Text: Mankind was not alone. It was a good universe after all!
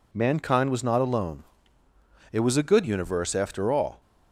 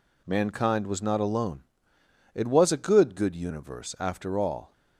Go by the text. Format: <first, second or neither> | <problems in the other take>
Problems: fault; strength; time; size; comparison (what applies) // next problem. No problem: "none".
first | says "good" twice; at 3.1 s